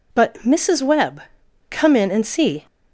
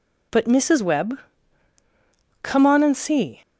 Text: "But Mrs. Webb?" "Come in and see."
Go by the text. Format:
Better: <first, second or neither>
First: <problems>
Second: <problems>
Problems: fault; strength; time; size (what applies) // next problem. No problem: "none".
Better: first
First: none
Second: says "on" for "in"; at 2.6 s